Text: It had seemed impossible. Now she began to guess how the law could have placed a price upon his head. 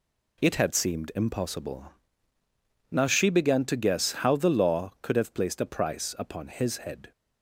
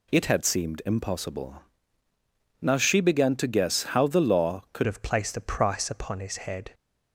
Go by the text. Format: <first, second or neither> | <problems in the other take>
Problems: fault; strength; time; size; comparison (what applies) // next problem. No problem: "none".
first | changes voice at "have"; from 4.8 s on; 1.9 s long